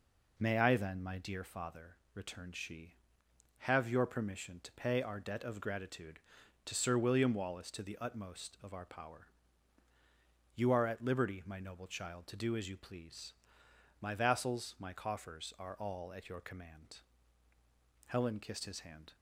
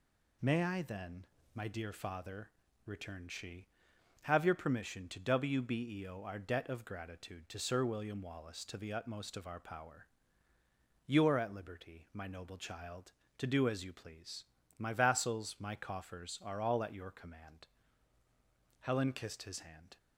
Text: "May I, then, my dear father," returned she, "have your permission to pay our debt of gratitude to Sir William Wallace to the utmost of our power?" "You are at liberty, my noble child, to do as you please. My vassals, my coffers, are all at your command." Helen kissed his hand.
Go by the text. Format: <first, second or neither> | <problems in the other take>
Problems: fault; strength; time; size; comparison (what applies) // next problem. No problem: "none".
first | says "wbeo" for "pay"; at 5.1 s